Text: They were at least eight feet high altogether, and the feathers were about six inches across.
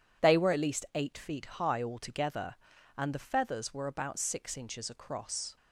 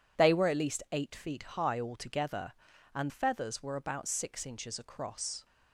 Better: first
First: none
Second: skips "the"; at 3.0 s

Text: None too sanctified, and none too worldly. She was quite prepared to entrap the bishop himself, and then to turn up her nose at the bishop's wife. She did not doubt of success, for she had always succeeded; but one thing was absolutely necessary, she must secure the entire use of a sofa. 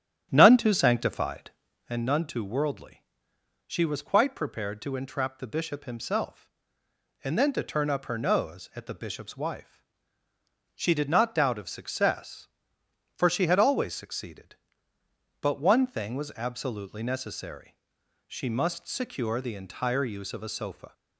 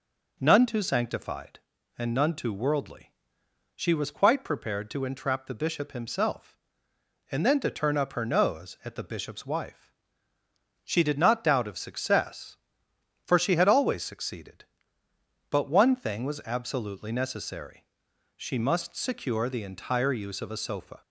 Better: second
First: starts louder than the rest; strong; until 2.0 s; 10 dB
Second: none

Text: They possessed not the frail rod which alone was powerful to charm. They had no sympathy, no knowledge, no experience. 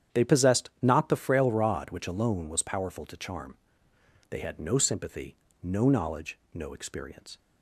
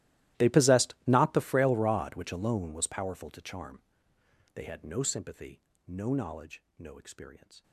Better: first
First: starts louder than the rest; strong; until 1.2 s; 9 dB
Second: gets quieter; strong; throughout; 23 dB // starts louder than the rest; strong; until 1.4 s; 15.5 dB

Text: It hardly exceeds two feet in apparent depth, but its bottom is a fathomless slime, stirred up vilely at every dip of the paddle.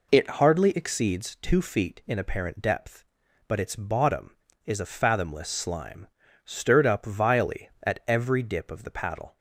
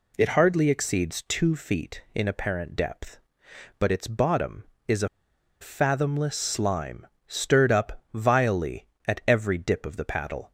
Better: first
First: none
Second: pauses between "a" and "fathomless"; noticeable; at 5.0 s; 0.53 s long

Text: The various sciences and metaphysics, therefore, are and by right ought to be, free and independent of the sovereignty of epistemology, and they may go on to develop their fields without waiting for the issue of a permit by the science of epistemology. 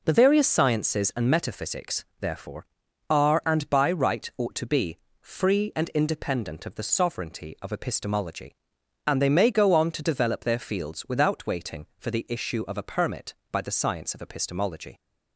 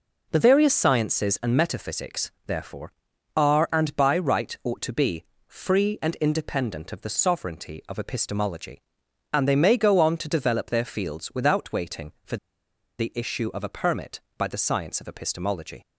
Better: first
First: none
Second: pauses between "for" and "the"; noticeable; at 12.3 s; 0.62 s long

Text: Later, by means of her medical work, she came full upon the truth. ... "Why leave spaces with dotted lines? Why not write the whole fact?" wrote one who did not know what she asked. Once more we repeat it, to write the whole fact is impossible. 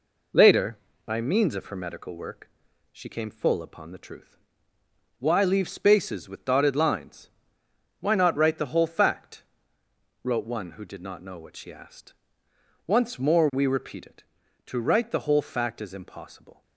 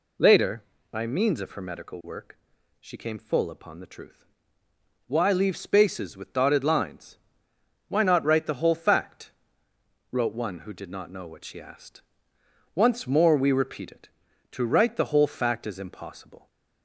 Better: second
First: gets quieter; throughout; 3.5 dB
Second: none

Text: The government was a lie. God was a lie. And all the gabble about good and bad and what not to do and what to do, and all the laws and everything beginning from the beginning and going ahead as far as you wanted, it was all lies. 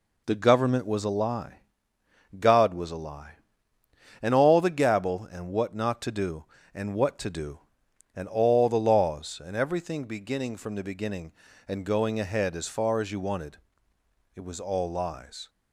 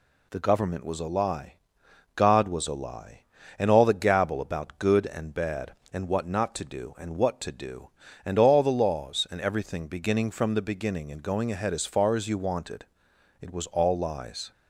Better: second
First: skips "about good and bad"; at 5.2 s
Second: none

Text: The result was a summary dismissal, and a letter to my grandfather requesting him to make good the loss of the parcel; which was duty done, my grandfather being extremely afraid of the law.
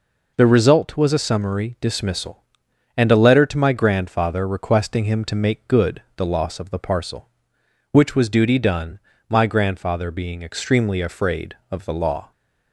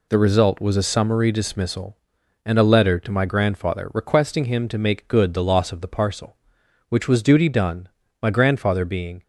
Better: first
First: none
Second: stops before "extremely afraid of the law"; at 9.2 s

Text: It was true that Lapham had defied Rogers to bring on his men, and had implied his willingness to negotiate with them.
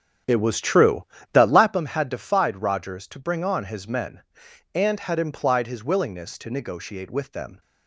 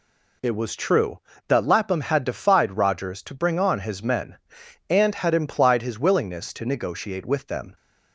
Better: second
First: starts louder than the rest; strong; until 1.8 s; 8.5 dB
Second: none

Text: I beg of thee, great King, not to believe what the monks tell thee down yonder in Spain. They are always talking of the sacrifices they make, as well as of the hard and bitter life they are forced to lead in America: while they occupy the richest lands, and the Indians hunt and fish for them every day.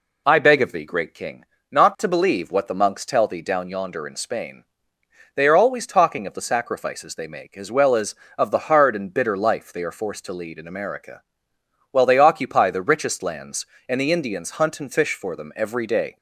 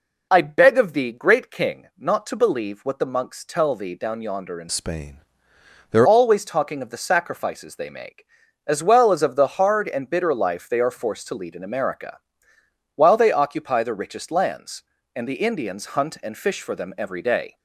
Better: first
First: none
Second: changes voice from "Spain" to "are"; from 4.6 to 6.0 s; 1.4 s long

